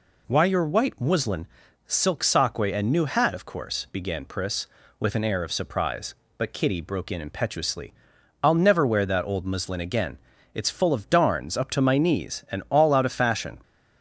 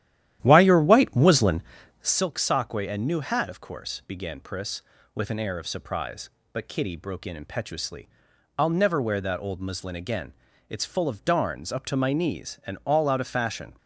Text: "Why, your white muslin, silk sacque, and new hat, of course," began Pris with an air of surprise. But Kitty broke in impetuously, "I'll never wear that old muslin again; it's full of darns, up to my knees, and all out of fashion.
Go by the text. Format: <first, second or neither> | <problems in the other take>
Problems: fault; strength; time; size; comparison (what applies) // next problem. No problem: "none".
first | starts louder than the rest; strong; until 2.3 s; 12 dB